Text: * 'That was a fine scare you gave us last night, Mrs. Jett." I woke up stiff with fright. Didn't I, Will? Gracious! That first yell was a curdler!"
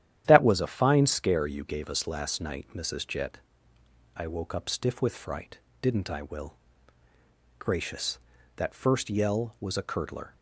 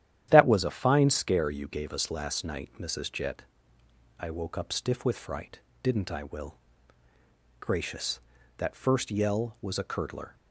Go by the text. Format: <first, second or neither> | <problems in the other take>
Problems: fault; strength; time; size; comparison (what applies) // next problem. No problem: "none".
neither | starts louder than the rest; strong; the same in both